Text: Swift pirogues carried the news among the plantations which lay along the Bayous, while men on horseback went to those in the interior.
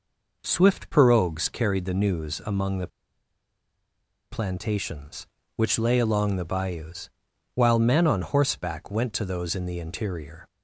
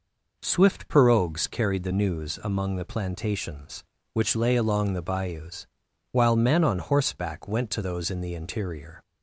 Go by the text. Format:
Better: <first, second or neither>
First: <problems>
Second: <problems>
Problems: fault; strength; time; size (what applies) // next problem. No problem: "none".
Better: second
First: pauses between "the" and "plantations"; strong; at 2.8 s; 1.4 s long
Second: none